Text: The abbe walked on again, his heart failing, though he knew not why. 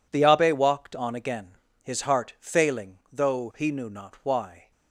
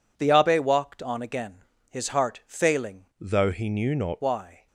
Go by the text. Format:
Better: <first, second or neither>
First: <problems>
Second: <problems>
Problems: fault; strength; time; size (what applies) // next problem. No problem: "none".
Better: first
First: none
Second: changes voice from "though" to "not"; from 3.2 to 4.2 s; 1.0 s long